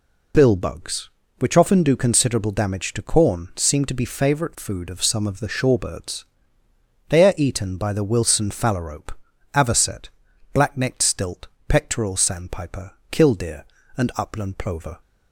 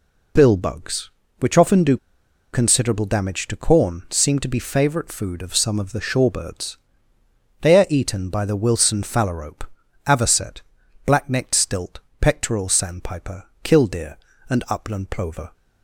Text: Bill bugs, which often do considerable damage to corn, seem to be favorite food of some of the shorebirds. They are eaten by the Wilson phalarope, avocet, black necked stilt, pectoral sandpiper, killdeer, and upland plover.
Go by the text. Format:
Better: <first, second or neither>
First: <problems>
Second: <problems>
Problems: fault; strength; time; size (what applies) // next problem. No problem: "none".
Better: first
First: none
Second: pauses between "do" and "considerable"; noticeable; at 1.9 s; 0.56 s long